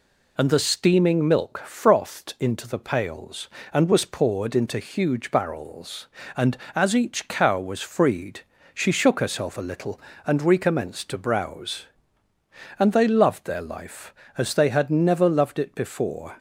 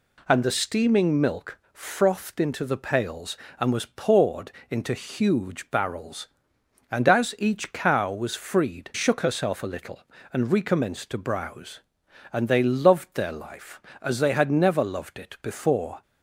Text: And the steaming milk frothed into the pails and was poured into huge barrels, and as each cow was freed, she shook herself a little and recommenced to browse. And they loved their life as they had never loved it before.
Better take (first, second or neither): first